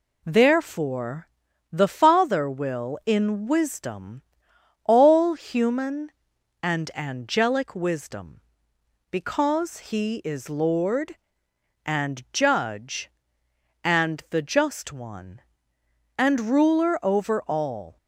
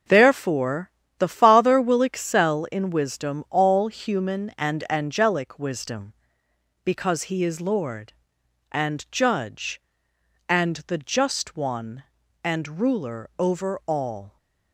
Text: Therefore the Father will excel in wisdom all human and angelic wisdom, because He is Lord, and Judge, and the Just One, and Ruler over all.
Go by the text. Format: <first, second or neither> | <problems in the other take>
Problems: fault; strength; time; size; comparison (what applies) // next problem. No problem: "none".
second | pauses between "Therefore" and "the"; at 1.2 s; 0.44 s long; slight in the second // skips "excel"; at 3.0 s // pauses between "wisdom" and "all"; noticeable; at 4.2 s; 0.64 s long